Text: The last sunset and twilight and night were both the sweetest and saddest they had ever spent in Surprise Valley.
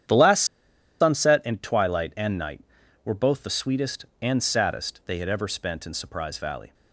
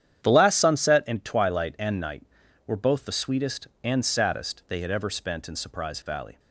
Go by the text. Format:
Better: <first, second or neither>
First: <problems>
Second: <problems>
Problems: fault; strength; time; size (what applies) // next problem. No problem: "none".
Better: second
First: starts louder than the rest; strong; until 1.7 s; 9.5 dB // pauses between "last" and "sunset"; noticeable; at 0.4 s; 0.56 s long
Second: starts louder than the rest; strong; until 1.3 s; 9.5 dB